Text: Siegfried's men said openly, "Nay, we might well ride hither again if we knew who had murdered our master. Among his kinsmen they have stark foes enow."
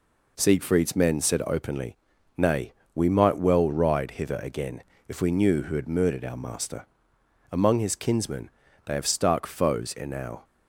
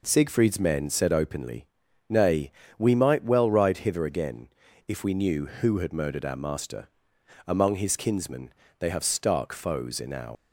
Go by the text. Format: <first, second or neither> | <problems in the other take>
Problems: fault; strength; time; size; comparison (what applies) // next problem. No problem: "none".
first | pauses between "again" and "if"; at 4.4 s; 0.38 s long; slight in the first // pauses between "kinsmen" and "they"; slight; at 8.5 s; 0.28 s long; slight in the first // leaves "enow" unfinished; at 10.3 s; 75 ms